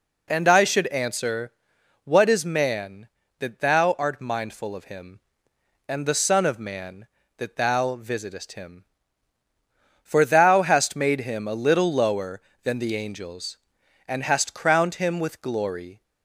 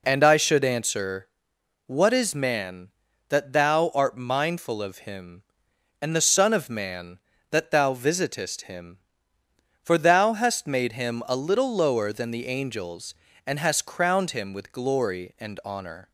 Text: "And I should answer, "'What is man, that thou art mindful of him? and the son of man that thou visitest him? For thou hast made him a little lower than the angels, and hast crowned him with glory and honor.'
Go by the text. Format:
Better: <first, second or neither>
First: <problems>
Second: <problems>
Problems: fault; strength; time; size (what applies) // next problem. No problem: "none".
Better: second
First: stops before "and honor"; at 16.0 s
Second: none